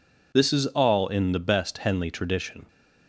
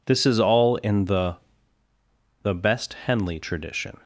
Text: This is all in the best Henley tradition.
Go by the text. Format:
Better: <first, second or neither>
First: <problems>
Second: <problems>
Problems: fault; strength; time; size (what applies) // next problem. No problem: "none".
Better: first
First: none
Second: says "the" twice; at 2.4 s